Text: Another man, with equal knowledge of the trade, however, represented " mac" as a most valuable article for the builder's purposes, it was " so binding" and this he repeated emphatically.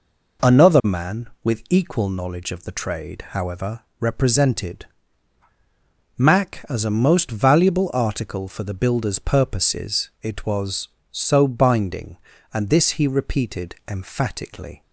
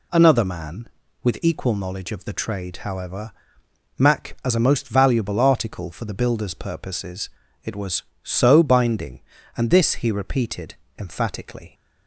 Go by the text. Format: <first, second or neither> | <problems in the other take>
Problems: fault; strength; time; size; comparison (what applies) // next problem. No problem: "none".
first | skips "represented"; at 3.4 s // pauses between "repeated" and "emphatically"; slight; at 10.7 s; 0.22 s long